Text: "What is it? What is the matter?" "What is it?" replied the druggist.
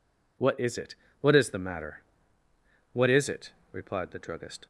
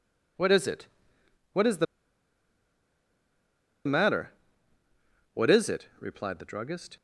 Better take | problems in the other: first | pauses between "the" and "matter"; strong; at 1.8 s; 2.0 s long

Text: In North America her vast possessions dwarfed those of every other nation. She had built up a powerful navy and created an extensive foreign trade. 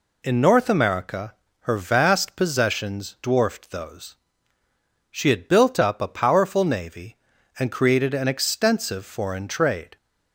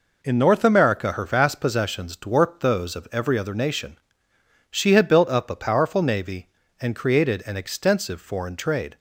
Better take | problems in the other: second | pauses between "America" and "her"; slight; at 1.3 s; 0.26 s long // skips "of every other nation"; at 4.6 s

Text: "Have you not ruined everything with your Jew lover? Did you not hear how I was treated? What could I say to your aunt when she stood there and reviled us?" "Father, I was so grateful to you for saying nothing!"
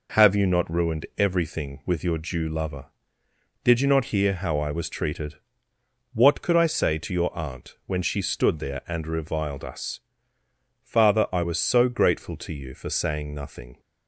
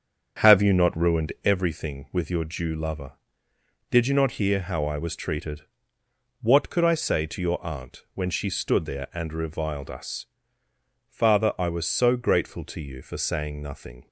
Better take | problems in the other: first | starts louder than the rest; strong; until 1.6 s; 7.5 dB

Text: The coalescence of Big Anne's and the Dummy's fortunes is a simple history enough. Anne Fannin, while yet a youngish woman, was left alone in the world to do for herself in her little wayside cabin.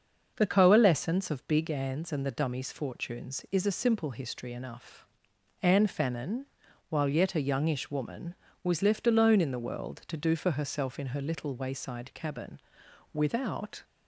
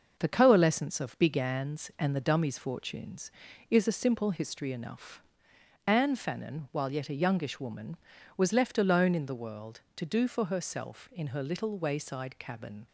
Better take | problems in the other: second | starts louder than the rest; until 1.3 s; 6.5 dB // goes on to say "Without"; noticeable; from 13.1 s on; 0.70 s long

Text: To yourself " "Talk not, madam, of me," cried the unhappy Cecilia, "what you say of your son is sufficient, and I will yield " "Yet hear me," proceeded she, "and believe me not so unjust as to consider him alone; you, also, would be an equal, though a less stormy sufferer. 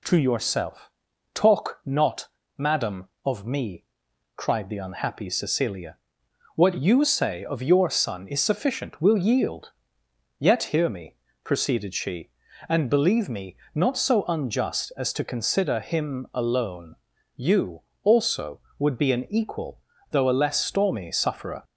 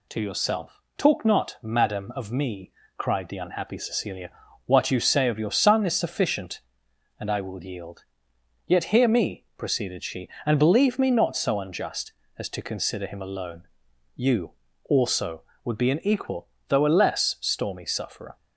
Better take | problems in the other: second | skips "and I"; at 8.9 s // pauses between "me" and "not"; slight; at 13.5 s; 0.18 s long

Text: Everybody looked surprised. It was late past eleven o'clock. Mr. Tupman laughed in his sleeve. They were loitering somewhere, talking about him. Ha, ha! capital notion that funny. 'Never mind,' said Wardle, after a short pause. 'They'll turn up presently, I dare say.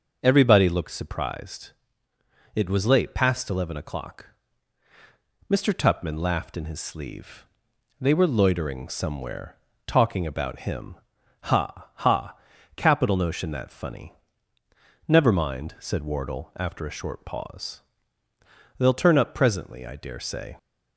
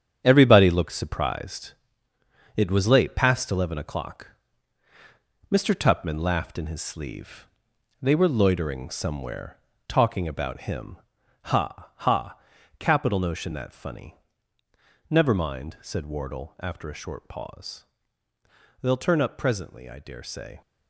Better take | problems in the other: first | gets quieter; strong; throughout; 9 dB

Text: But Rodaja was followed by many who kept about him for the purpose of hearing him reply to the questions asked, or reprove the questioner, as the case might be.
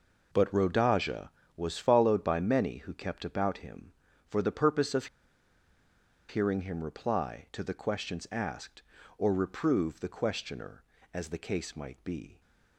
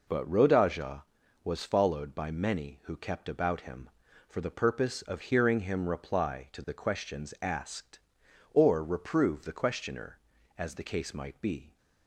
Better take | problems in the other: second | pauses between "of" and "hearing"; at 5.0 s; 1.2 s long

